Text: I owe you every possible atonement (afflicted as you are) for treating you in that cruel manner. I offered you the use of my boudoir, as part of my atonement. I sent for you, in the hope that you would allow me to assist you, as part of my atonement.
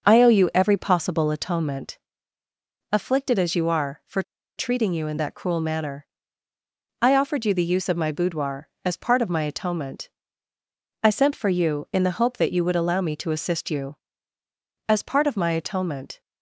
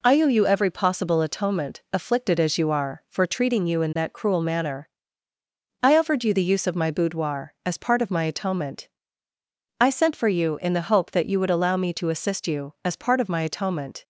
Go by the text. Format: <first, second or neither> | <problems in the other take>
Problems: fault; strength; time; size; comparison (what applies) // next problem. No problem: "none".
second | pauses between "for" and "treating"; slight; at 4.2 s; 0.35 s long